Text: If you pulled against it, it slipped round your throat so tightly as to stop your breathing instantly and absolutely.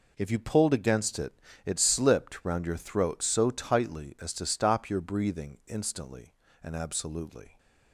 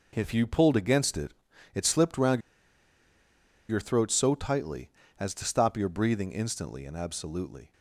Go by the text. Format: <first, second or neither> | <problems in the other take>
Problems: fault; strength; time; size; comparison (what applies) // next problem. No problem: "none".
first | pauses between "round" and "your"; strong; at 2.3 s; 1.2 s long